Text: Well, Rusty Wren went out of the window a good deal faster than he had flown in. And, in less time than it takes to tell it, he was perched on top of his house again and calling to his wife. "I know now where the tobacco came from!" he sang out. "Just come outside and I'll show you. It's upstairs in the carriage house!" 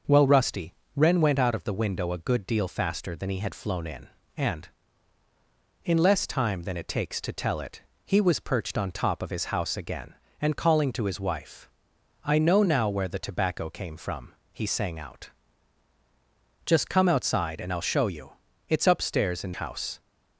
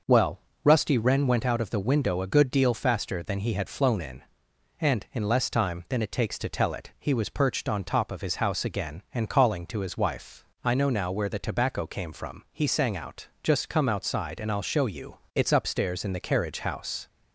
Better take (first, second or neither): second